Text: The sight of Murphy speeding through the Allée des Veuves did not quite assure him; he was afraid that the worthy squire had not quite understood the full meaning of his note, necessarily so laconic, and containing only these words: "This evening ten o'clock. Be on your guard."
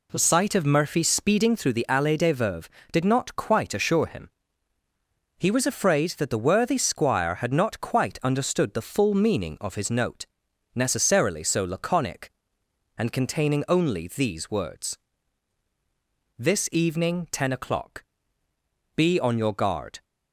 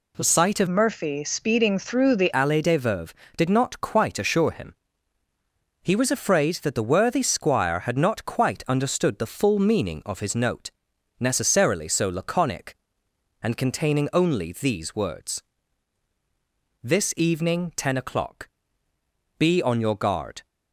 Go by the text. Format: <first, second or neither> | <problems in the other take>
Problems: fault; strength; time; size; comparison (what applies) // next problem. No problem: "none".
first | changes voice from "Murphy" to "the"; from 0.6 to 2.3 s; 1.7 s long